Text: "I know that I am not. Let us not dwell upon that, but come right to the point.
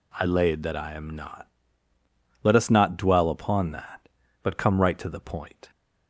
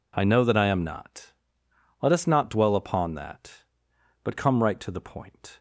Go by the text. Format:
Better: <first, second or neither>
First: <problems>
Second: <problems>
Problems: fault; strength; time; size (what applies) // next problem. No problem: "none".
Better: second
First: says "laid" for "know"; at 0.2 s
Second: none